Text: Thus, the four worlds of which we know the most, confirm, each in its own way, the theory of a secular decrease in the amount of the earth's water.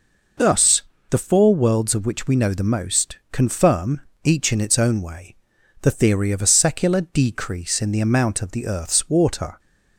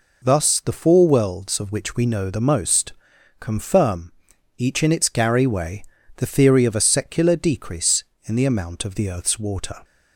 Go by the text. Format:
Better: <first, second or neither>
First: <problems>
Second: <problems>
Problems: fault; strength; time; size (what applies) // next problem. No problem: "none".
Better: first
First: none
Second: says "gary" for "own"; at 5.0 s